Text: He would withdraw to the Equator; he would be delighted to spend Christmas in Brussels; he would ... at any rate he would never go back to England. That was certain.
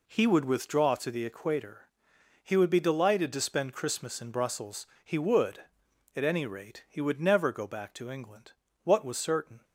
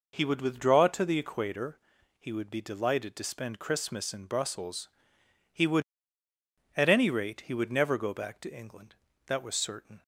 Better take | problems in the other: second | says "What" for "That"; at 8.8 s

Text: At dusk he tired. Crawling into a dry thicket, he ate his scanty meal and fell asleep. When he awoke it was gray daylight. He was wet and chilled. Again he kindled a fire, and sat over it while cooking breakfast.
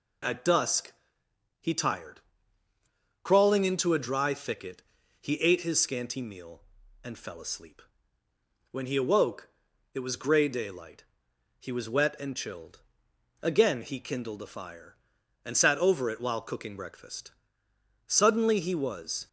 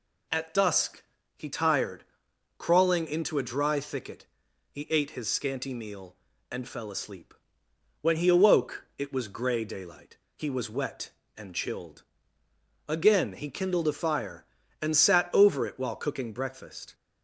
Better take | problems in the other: second | pauses between "dusk" and "he"; noticeable; at 0.9 s; 0.66 s long; slight in the second // pauses between "awoke" and "it"; at 9.4 s; 0.44 s long // goes on to say "Suddenly he was"; noticeable; from 18.0 s on; 1.2 s long

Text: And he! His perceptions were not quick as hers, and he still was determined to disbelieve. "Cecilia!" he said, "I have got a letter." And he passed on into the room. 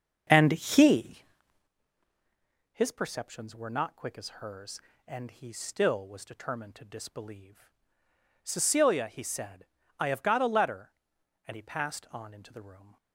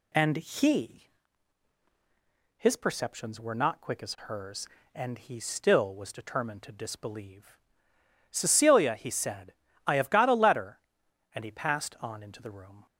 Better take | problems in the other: second | starts louder than the rest; until 1.7 s; 7 dB

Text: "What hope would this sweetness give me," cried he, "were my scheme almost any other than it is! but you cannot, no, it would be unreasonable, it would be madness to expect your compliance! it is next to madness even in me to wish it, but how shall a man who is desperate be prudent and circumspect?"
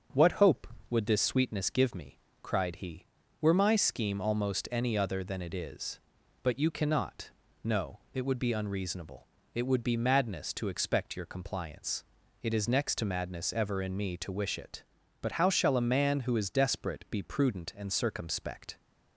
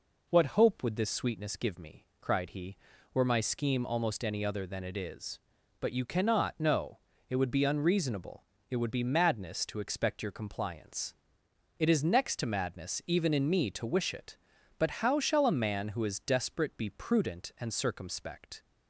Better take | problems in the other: second | starts louder than the rest; strong; until 1.3 s; 7.5 dB // says "ever" for "even"; at 13.5 s

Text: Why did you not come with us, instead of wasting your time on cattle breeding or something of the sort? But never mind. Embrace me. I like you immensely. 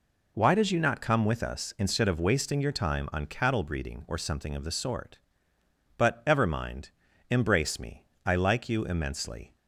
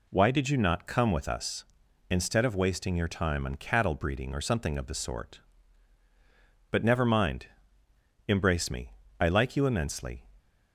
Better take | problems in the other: second | says "ever" for "never"; at 6.2 s

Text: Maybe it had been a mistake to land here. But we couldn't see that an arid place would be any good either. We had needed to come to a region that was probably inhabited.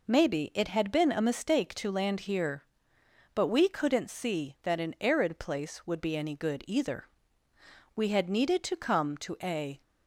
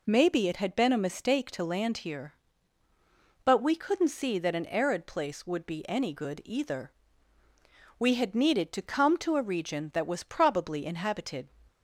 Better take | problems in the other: second | stops before "region that was probably inhabited"; at 9.8 s

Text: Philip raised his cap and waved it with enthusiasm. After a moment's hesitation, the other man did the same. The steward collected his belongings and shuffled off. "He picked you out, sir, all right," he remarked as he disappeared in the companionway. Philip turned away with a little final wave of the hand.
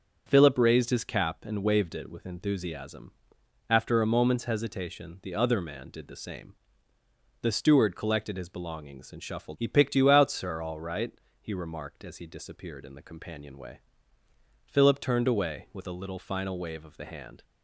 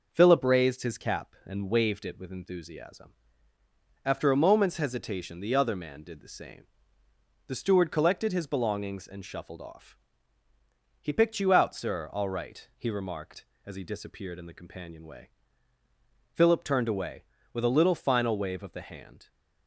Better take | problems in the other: second | starts louder than the rest; until 1.2 s; 7 dB // skips "off"; at 9.5 s

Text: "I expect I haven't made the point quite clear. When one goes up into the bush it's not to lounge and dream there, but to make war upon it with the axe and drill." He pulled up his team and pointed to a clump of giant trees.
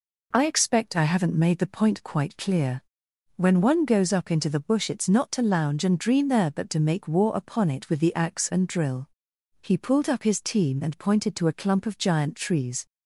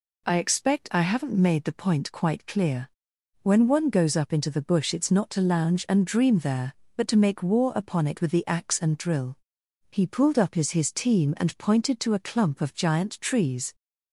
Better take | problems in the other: first | says "his" twice; at 10.7 s

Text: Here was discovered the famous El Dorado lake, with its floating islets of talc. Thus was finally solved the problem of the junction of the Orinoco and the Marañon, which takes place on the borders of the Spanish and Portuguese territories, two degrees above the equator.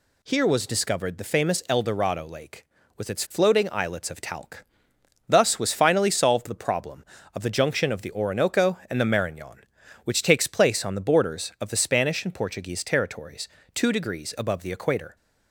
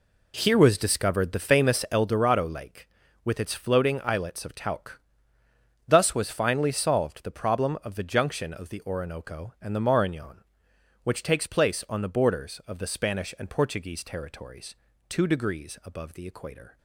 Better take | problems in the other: first | starts louder than the rest; slight; until 2.1 s; 3 dB

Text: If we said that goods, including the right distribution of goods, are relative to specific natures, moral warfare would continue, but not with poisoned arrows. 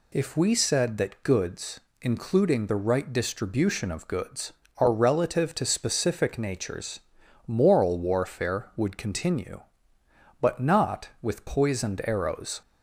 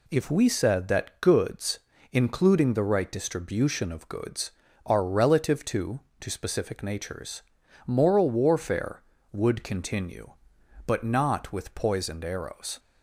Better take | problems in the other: first | says "to" twice; at 6.2 s

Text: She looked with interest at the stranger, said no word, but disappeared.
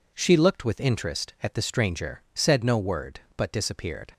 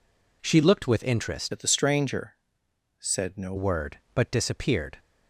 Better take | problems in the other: first | changes voice from "at" to "no"; from 1.5 to 3.5 s; 2.0 s long

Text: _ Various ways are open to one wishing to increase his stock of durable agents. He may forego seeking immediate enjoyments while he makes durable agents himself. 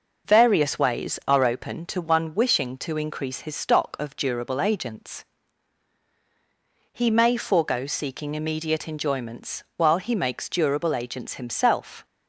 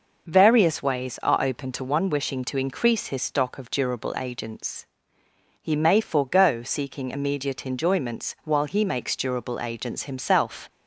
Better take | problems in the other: neither | none

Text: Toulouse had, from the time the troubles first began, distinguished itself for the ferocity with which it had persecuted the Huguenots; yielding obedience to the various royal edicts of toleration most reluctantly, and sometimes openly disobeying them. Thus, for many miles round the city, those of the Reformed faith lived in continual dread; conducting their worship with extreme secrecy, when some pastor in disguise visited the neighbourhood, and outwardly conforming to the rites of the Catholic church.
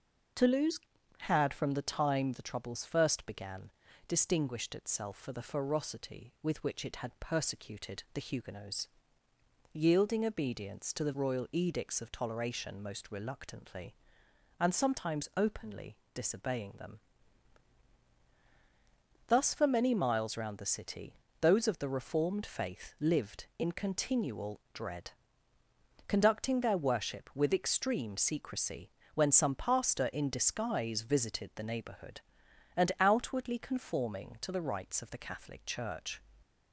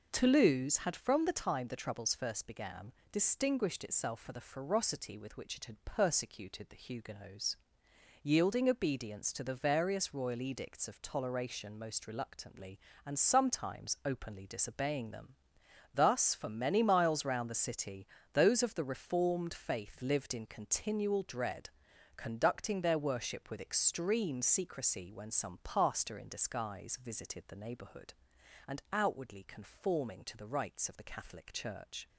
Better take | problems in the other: second | starts louder than the rest; until 1.7 s; 6.5 dB // skips "various"; at 11.1 s // pauses between "openly" and "disobeying"; slight; at 15.9 s; 0.18 s long

